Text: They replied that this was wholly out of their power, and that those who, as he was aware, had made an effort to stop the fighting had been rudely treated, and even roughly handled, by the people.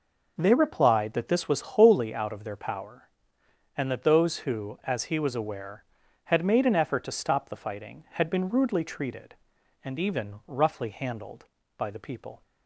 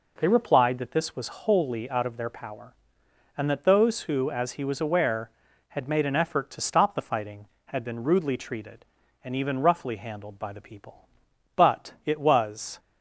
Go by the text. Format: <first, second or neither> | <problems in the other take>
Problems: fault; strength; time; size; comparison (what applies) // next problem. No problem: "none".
first | goes on to say "But it was"; noticeable; from 11.5 s on; 1.2 s long